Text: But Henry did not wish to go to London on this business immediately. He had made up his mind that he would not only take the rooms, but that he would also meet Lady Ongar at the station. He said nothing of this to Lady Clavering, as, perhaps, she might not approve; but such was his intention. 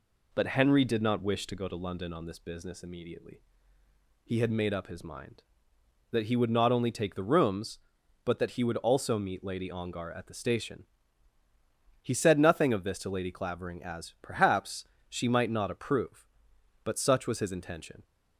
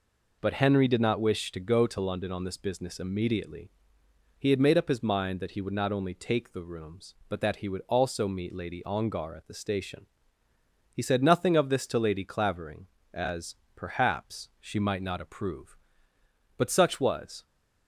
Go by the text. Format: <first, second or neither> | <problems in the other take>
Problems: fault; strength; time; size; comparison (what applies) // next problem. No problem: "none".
first | stops before "his intention"; at 17.4 s